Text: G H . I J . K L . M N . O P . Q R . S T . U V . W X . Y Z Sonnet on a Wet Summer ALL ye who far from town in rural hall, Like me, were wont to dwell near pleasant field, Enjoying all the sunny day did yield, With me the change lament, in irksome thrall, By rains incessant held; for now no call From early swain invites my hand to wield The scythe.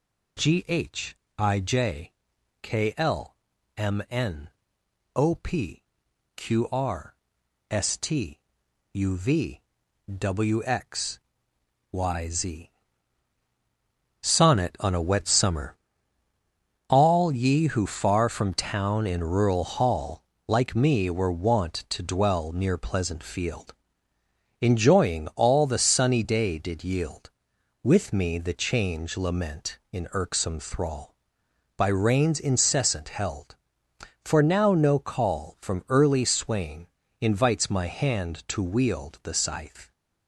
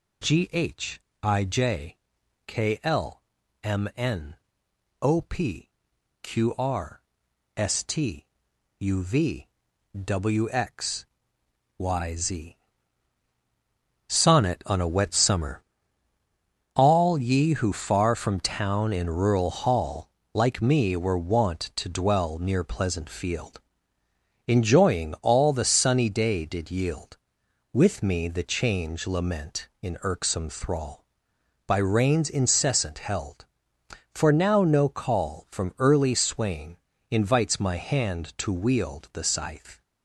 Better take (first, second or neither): neither